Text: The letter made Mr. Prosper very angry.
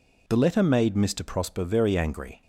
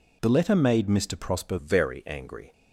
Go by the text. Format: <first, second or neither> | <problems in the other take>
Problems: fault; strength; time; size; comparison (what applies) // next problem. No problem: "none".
first | changes voice at "very"; from 1.5 s on; 1.0 s long